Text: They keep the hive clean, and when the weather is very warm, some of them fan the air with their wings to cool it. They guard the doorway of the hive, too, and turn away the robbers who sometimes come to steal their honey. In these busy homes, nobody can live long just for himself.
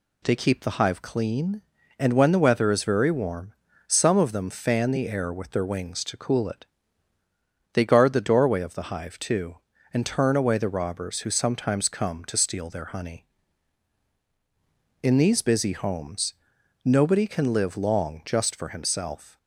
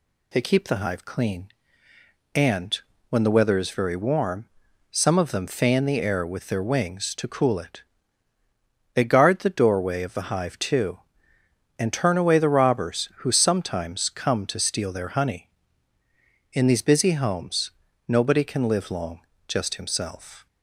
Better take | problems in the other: first | pauses between "and" and "when"; slight; at 2.7 s; 0.32 s long // pauses between "long" and "just"; slight; at 19.2 s; 0.26 s long // skips "for"; at 19.7 s

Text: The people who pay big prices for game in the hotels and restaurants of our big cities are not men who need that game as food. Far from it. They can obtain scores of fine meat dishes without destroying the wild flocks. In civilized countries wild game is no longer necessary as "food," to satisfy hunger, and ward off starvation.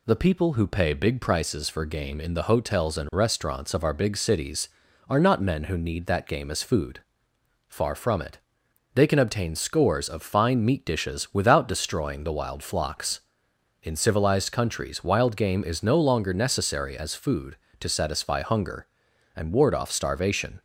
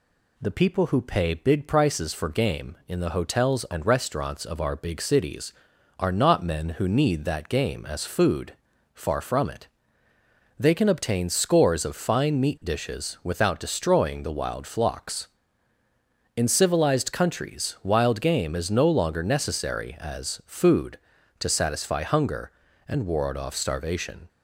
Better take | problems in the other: neither | none

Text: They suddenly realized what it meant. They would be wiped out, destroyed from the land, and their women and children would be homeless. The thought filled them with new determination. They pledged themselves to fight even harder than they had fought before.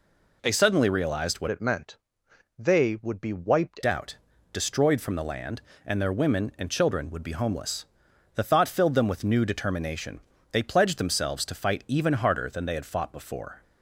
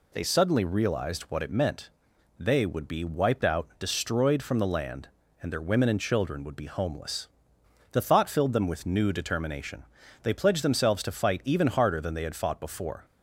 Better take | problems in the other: second | changes voice from "it" to "wiped"; from 1.5 to 3.8 s; 2.3 s long

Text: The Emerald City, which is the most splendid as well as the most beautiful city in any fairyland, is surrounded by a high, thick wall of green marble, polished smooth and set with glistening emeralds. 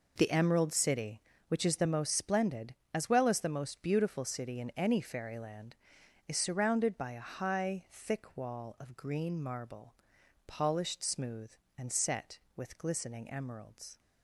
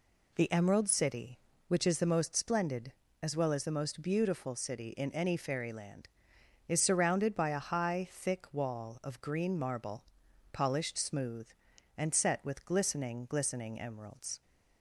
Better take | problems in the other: first | says "glistening" twice; at 13.2 s

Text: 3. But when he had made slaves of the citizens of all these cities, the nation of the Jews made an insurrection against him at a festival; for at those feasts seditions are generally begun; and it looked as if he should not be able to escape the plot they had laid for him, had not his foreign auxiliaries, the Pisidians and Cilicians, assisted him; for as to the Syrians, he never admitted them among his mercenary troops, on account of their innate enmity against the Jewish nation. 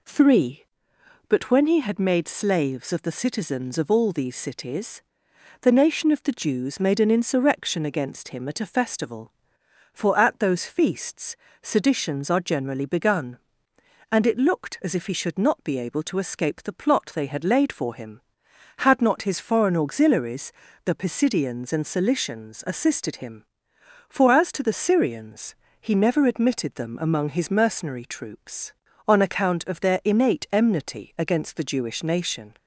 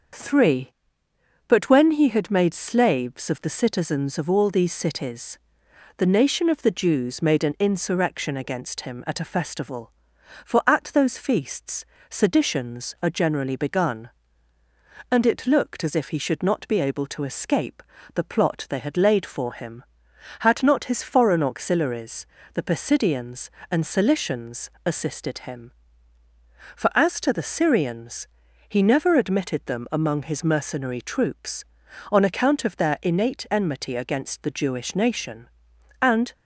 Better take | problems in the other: first | starts louder than the rest; until 1.9 s; 6.5 dB // pauses between "feasts" and "seditions"; slight; at 11.8 s; 0.24 s long; slight in the first // pauses between "escape" and "the"; slight; at 17.8 s; 0.32 s long // goes on to say "And"; slight; from 36.0 s on; 0.32 s long

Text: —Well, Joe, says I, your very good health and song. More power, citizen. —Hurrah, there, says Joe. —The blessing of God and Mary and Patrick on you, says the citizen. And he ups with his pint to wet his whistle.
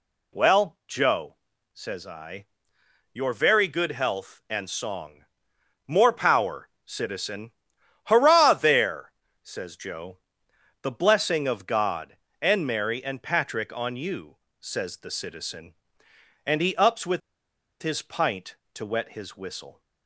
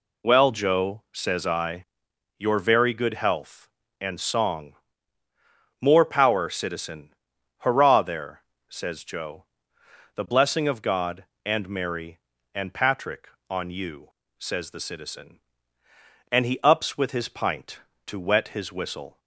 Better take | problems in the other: second | pauses between "with" and "his"; noticeable; at 17.2 s; 0.61 s long

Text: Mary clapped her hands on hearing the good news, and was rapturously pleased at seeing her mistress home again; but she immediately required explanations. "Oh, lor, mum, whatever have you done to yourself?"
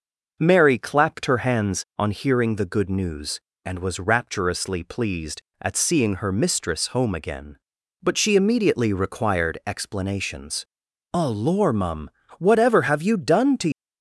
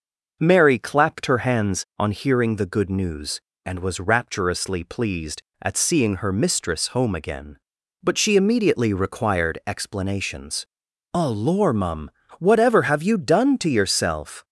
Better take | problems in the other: second | stops before "yourself"; at 13.7 s

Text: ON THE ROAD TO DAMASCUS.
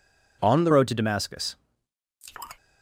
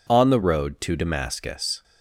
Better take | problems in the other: second | changes voice at "ROAD"; from 0.7 s on; 0.8 s long

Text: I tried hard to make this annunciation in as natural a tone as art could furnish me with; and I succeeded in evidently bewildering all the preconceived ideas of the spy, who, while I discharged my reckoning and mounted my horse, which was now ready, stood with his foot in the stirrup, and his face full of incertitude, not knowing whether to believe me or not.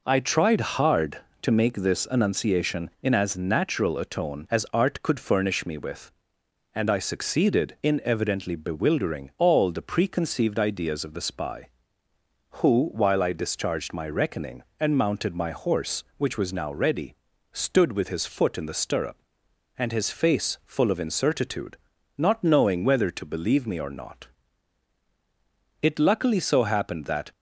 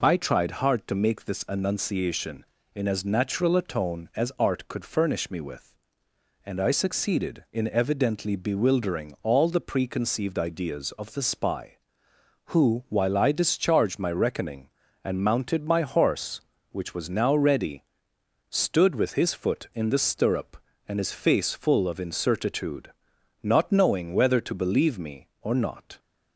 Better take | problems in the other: second | goes on to say "It luckily so happened that"; from 25.7 s on; 1.5 s long

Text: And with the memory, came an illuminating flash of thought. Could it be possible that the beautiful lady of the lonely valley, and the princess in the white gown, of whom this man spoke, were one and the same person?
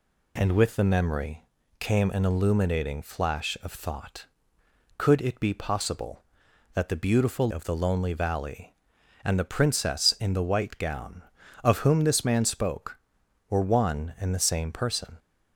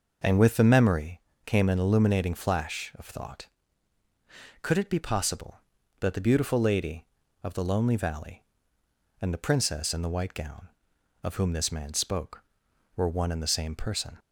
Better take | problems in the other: second | skips "lady"; at 7.4 s

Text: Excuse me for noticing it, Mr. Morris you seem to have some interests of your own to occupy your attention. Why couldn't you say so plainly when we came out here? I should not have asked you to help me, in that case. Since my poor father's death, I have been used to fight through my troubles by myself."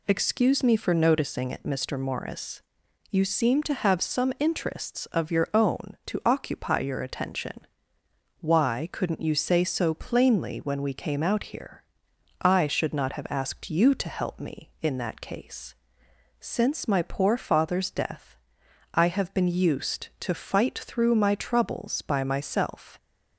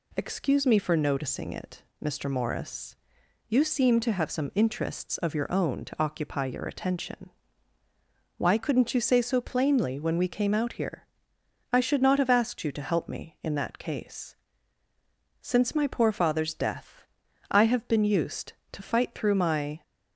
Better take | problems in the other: first | pauses between "Morris" and "you"; noticeable; at 2.9 s; 0.52 s long; noticeable in the first // stops before "troubles by myself"; at 19.8 s

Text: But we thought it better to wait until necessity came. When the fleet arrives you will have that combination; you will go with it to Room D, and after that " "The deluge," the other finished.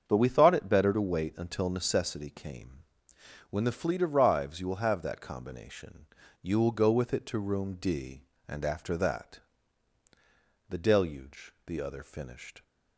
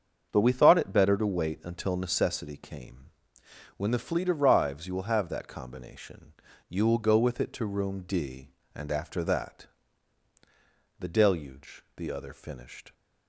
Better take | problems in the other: neither | starts louder than the rest; strong; the same in both

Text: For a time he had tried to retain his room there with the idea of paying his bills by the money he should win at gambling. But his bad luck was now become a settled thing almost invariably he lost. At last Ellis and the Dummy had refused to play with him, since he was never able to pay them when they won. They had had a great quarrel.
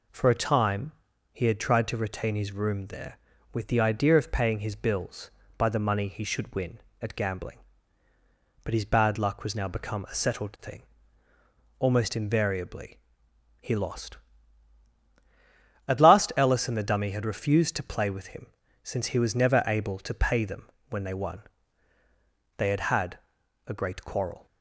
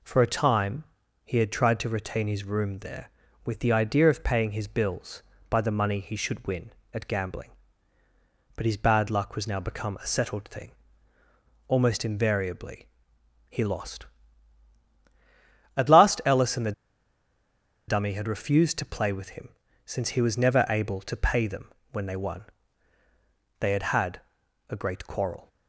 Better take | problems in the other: first | pauses between "time" and "he"; at 0.8 s; 0.40 s long; also in the first // pauses between "thing" and "almost"; noticeable; at 10.7 s; 0.96 s long; noticeable in the first // pauses between "invariably" and "he"; noticeable; at 12.8 s; 0.62 s long; noticeable in the first // pauses between "the" and "Dummy"; at 16.7 s; 1.1 s long // pauses between "them" and "when"; slight; at 21.7 s; 0.22 s long; slight in the first // pauses between "had" and "a"; noticeable; at 24.1 s; 0.50 s long; noticeable in the first

